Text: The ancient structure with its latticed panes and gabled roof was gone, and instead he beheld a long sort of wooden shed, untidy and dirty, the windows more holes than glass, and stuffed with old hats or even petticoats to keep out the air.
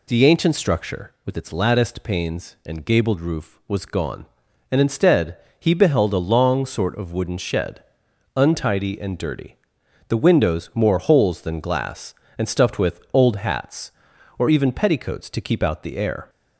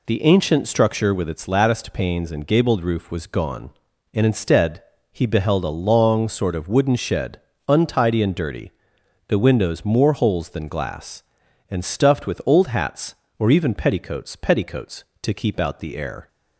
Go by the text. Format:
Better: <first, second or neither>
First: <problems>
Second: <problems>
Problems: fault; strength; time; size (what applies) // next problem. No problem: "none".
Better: first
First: pauses between "instead" and "he"; slight; at 5.3 s; 0.22 s long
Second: pauses between "instead" and "he"; slight; at 4.8 s; 0.28 s long // says "petticoats" twice; at 14.3 s